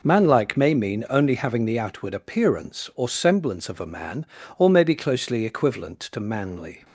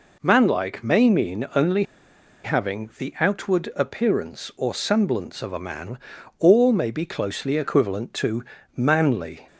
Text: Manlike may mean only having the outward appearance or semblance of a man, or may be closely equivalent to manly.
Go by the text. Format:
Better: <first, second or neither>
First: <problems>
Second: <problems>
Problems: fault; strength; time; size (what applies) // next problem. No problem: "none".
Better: first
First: none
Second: pauses between "only" and "having"; noticeable; at 1.8 s; 0.60 s long // pauses between "to" and "manly"; slight; at 8.4 s; 0.32 s long